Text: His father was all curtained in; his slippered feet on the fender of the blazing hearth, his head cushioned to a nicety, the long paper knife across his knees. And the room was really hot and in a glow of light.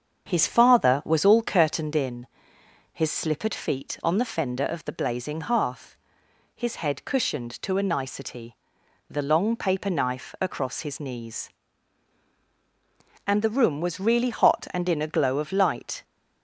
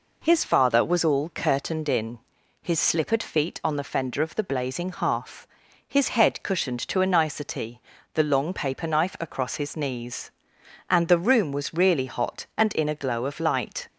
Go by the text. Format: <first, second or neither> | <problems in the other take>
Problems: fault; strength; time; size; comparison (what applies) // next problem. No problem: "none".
second | starts louder than the rest; until 2.0 s; 7 dB